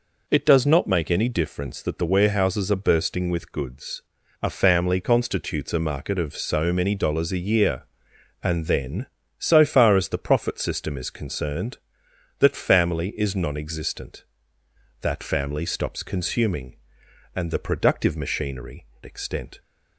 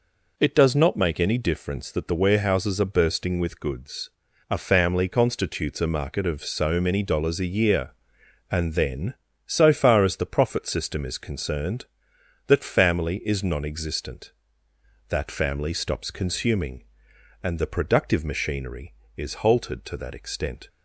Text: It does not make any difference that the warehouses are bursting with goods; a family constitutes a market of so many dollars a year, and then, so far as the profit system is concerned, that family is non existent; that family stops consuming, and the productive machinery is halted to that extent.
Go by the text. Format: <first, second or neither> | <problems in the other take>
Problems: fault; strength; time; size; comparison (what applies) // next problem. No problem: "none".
second | skips "is halted to that"; at 18.9 s